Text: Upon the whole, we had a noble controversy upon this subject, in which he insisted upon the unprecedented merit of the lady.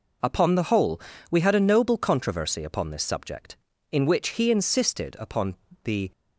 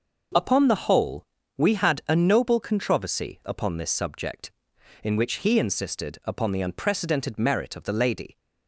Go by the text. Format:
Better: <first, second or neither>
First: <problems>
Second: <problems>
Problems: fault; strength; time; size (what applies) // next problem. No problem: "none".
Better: second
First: pauses between "upon" and "the"; slight; at 5.5 s; 0.28 s long // stops before "unprecedented merit of the lady"; at 6.1 s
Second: none